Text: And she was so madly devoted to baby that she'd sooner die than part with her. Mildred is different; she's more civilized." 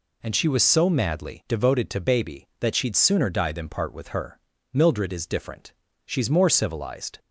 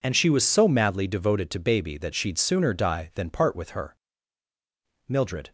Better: first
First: none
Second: stops before "is different she's more civilized"; at 5.4 s

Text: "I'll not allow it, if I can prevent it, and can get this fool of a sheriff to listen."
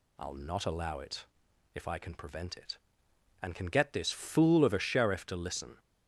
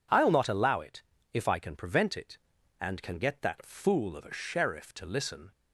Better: first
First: none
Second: says "that" for "this"; at 3.4 s

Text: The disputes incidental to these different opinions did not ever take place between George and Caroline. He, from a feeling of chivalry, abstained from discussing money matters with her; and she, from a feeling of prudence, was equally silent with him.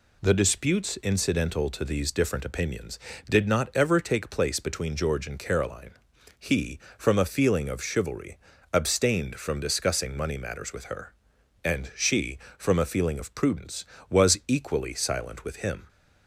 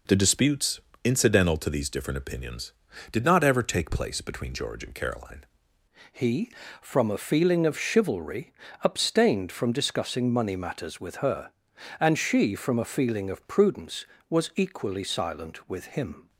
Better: first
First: none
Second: pauses between "disputes" and "incidental"; slight; at 0.7 s; 0.24 s long // changes voice at "He"; from 6.1 s on; 10.1 s long

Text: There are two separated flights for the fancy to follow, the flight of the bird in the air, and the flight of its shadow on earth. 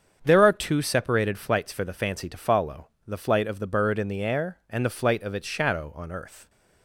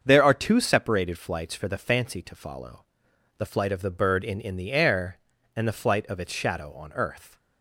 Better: first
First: starts louder than the rest; strong; until 1.2 s; 7.5 dB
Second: starts louder than the rest; until 1.0 s; 7 dB // says "in" twice; at 4.4 s

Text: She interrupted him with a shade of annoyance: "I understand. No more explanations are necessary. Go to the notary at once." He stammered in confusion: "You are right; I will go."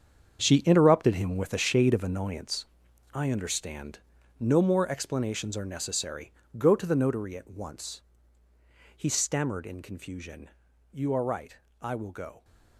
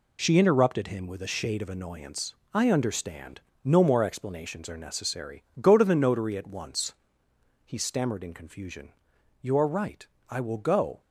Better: second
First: gets quieter; strong; throughout; 12 dB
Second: none

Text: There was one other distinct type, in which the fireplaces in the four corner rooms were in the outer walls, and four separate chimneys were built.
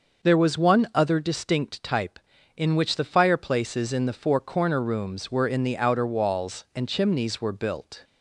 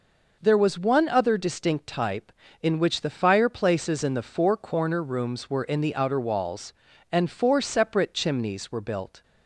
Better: second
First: skips "four separate"; at 6.8 s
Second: none

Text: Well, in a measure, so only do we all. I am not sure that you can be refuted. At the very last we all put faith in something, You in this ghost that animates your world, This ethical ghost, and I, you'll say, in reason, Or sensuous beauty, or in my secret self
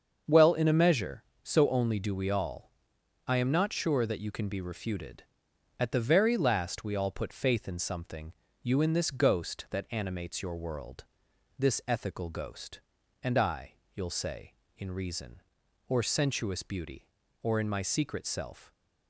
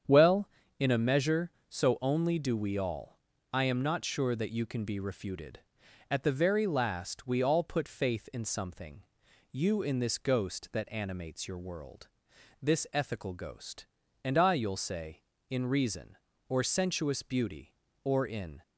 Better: first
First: starts louder than the rest; until 1.4 s; 7 dB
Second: starts louder than the rest; strong; until 1.3 s; 8.5 dB // stops before "my secret self"; at 18.6 s

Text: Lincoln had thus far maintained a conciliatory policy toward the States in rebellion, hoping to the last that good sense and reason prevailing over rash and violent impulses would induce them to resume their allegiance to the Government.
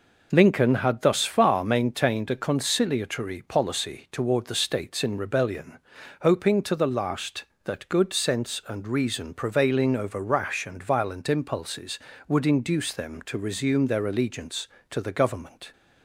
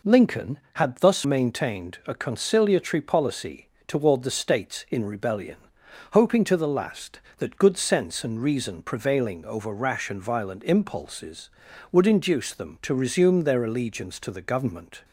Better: first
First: none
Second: skips "far"; at 1.2 s // pauses between "policy" and "toward"; slight; at 3.7 s; 0.16 s long

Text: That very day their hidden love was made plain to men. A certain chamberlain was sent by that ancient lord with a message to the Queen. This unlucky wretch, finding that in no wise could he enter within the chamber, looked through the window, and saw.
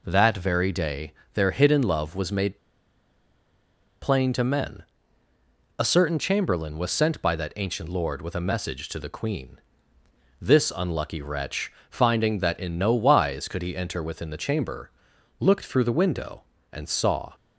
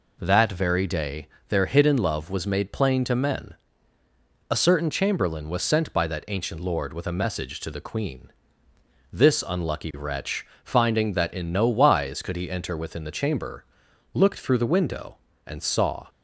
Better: second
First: pauses between "day" and "their"; slight; at 1.1 s; 0.20 s long // pauses between "made" and "plain"; strong; at 2.5 s; 1.4 s long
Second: pauses between "day" and "their"; slight; at 1.2 s; 0.20 s long

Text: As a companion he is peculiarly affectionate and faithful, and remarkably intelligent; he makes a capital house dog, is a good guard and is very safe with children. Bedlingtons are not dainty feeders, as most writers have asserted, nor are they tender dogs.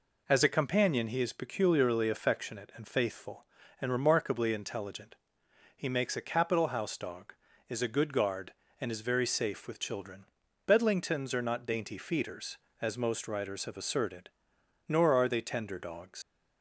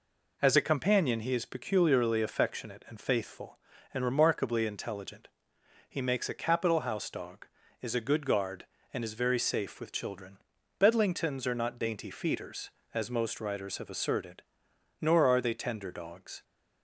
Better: second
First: leaves "dogs" unfinished; at 16.2 s; 80 ms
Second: none

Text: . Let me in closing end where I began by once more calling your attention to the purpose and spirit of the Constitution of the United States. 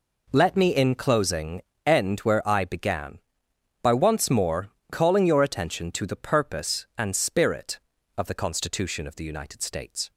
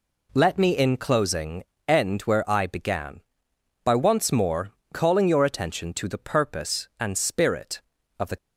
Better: first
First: pauses between "closing" and "end"; slight; at 1.6 s; 0.24 s long // pauses between "more" and "calling"; slight; at 4.6 s; 0.22 s long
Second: pauses between "closing" and "end"; slight; at 1.6 s; 0.24 s long // pauses between "more" and "calling"; slight; at 4.7 s; 0.22 s long // stops before "Constitution of the United States"; at 8.3 s

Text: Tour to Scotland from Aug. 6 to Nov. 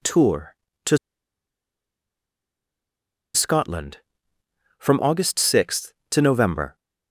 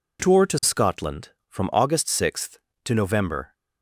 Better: second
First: pauses between "to" and "Scotland"; strong; at 0.9 s; 2.3 s long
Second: none

